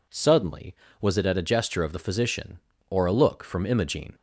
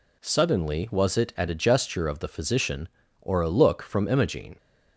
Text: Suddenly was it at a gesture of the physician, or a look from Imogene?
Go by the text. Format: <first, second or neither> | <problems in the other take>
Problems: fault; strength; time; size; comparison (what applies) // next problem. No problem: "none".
neither | none